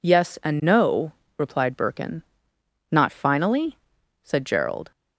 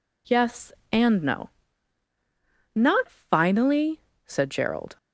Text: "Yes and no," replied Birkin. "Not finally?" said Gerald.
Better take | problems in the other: first | skips "replied Birkin"; at 2.1 s

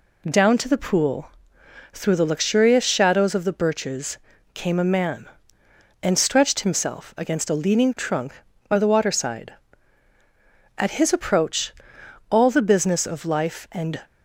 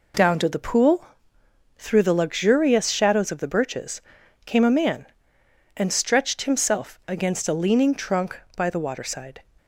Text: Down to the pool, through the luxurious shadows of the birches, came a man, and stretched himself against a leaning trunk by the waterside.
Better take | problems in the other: second | goes on to say "At his approach all the business of life and"; strong; from 10.7 s on; 3.2 s long

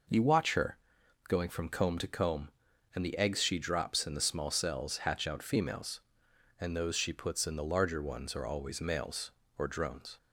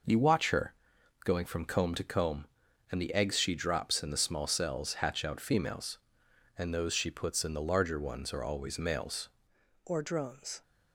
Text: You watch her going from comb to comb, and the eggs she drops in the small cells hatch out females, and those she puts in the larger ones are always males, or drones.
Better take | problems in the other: first | pauses between "her" and "going"; noticeable; at 0.7 s; 0.50 s long; noticeable in the first // changes voice at "or"; from 9.8 s on; 0.8 s long

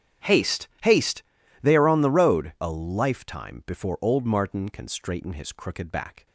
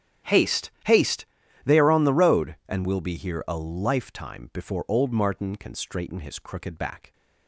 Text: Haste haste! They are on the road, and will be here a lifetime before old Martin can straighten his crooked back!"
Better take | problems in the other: second | starts louder than the rest; strong; until 1.8 s; 9.5 dB; strong in the second // pauses between "Haste" and "haste"; slight; at 0.6 s; 0.16 s long; slight in the second // skips "and will be here"; at 2.5 s

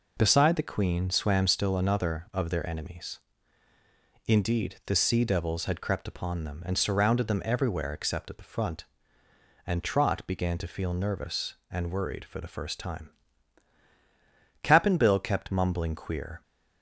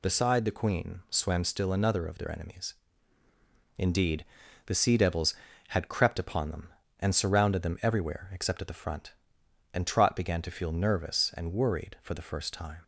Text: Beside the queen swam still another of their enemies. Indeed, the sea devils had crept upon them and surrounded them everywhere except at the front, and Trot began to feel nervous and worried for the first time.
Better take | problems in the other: second | goes on to say "Cap'n Bill kept mumbling queer"; strong; from 14.6 s on; 1.7 s long

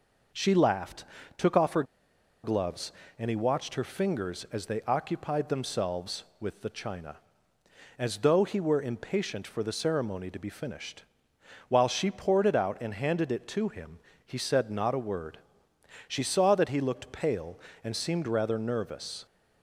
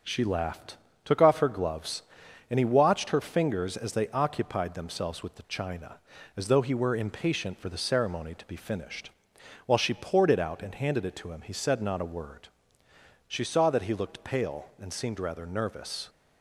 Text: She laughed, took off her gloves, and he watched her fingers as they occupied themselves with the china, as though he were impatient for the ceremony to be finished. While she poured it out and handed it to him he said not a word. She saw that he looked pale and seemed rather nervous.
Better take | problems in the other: second | pauses between "her" and "gloves"; noticeable; at 1.8 s; 0.59 s long // pauses between "him" and "he"; slight; at 13.9 s; 0.26 s long

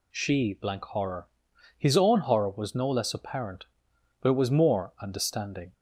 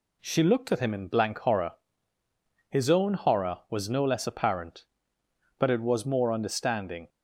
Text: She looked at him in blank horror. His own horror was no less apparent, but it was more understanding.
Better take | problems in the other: second | skips "looked at him in"; at 0.5 s

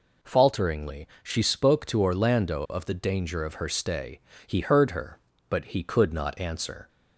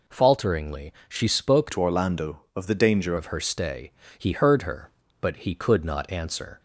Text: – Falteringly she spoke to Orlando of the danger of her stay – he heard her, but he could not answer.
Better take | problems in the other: first | pauses between "Falteringly" and "she"; slight; at 0.9 s; 0.16 s long; slight in the first // changes voice from "to" to "danger"; from 1.7 to 3.1 s; 1.4 s long

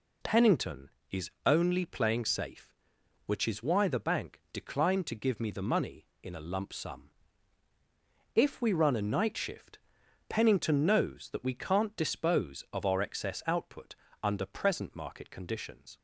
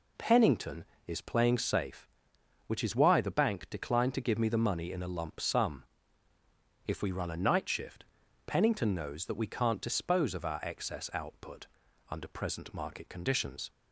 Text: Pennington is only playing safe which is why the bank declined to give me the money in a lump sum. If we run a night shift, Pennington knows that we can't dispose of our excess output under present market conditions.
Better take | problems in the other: first | skips "only"; at 1.2 s // pauses between "output" and "under"; at 11.6 s; 0.42 s long; slight in the first

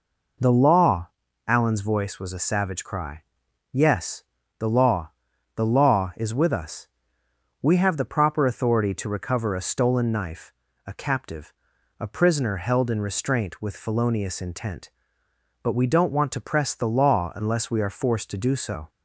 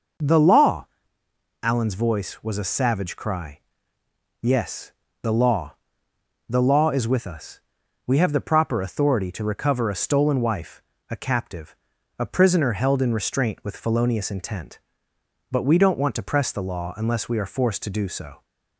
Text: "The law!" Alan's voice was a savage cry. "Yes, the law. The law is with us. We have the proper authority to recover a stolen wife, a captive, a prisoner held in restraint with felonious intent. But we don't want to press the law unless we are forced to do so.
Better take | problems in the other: second | says "knife" for "wife"; at 10.1 s

